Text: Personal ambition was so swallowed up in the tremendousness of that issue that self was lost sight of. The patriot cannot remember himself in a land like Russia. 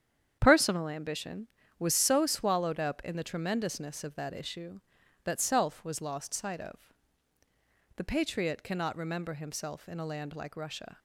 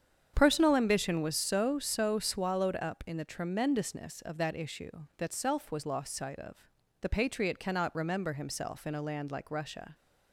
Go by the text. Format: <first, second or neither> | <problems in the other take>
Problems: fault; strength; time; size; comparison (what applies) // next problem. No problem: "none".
first | starts louder than the rest; strong; until 1.3 s; 8 dB; strong in the first // says "so" twice; at 1.7 s